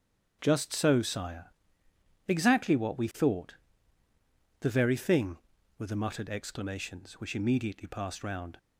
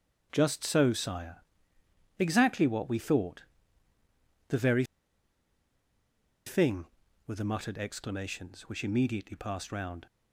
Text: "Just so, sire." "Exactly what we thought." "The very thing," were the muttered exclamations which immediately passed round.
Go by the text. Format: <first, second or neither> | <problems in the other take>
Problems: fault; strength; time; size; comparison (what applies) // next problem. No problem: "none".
first | starts louder than the rest; strong; until 1.3 s; 8 dB; strong in the first // pauses between "very" and "thing"; strong; at 4.8 s; 1.6 s long